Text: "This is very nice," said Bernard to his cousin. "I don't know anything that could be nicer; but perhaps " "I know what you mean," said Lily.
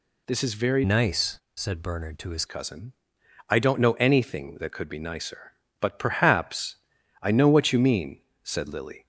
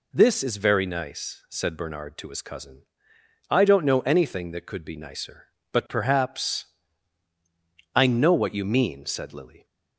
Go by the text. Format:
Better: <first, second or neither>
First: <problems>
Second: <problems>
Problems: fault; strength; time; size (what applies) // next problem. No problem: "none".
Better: second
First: changes voice from "nice" to "his"; from 0.8 to 2.4 s; 1.6 s long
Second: none